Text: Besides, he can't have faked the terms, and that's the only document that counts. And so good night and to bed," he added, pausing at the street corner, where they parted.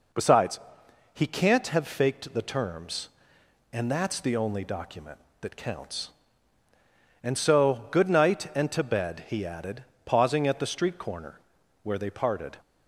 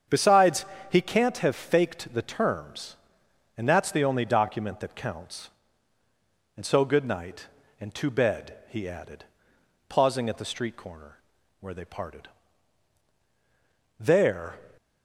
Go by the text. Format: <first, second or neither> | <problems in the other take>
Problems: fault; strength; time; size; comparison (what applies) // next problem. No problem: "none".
first | starts louder than the rest; strong; until 1.3 s; 7.5 dB // goes on to say "There"; from 13.9 s on; 0.60 s long